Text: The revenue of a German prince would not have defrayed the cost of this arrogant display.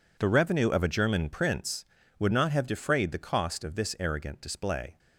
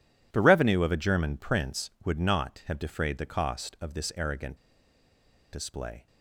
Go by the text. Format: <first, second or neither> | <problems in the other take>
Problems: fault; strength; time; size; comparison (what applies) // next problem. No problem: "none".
first | pauses between "arrogant" and "display"; noticeable; at 4.5 s; 0.98 s long